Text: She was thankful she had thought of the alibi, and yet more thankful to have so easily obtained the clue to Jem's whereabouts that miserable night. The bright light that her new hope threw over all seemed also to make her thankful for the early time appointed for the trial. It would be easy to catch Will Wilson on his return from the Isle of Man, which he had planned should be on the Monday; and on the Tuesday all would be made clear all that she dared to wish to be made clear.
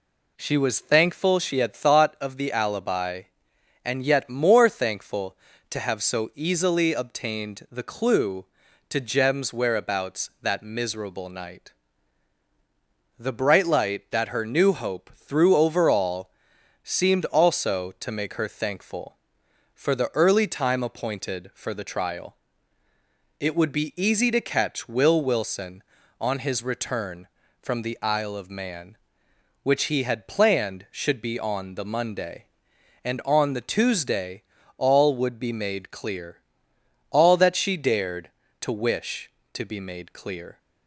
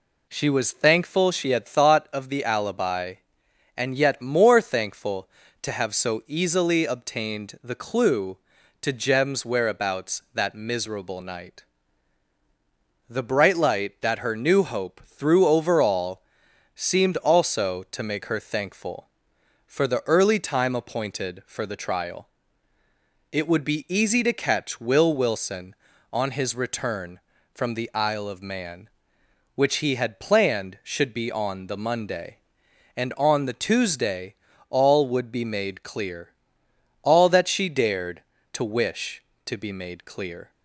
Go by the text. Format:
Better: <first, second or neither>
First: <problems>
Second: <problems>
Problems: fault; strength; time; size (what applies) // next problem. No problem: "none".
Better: neither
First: pauses between "all" and "seemed"; noticeable; at 16.3 s; 0.52 s long // pauses between "Tuesday" and "all"; slight; at 34.4 s; 0.36 s long // pauses between "clear" and "all"; noticeable; at 36.3 s; 0.72 s long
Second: pauses between "all" and "seemed"; noticeable; at 16.2 s; 0.52 s long // pauses between "Tuesday" and "all"; slight; at 34.3 s; 0.36 s long // pauses between "clear" and "all"; noticeable; at 36.2 s; 0.72 s long